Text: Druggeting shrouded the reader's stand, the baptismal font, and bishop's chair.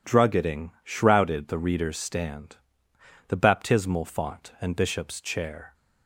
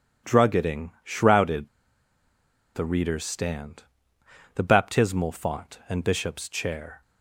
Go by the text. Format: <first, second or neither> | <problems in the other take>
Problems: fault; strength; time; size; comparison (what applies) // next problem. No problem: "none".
first | pauses between "shrouded" and "the"; at 1.6 s; 1.0 s long